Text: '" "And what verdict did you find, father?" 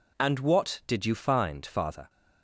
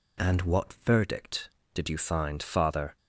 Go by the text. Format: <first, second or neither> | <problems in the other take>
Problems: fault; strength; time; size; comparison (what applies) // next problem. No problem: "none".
second | skips "verdict"; at 0.8 s